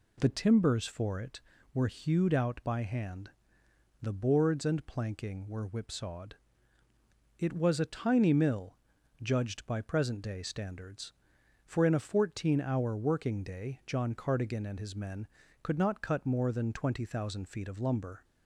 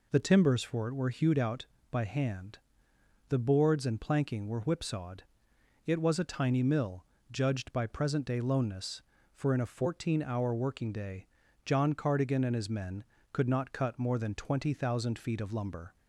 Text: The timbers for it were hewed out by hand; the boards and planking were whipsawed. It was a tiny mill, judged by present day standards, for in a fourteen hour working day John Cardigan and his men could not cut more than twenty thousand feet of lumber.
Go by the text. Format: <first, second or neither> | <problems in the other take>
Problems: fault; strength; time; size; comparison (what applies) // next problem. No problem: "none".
first | says "loneness" for "standards"; at 8.3 s // pauses between "day" and "John"; at 11.2 s; 0.38 s long